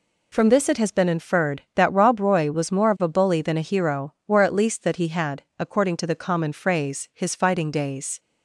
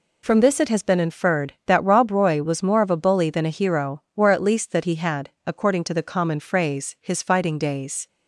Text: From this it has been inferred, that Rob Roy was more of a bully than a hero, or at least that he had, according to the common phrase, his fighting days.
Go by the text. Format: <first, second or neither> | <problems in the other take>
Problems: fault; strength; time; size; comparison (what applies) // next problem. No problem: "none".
neither | none